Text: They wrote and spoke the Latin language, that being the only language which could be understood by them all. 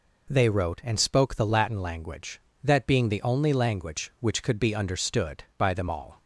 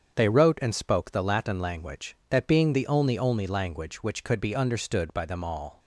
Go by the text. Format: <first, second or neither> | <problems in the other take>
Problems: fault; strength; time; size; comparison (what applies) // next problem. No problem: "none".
first | starts louder than the rest; strong; until 1.1 s; 7.5 dB // says "only" twice; at 3.1 s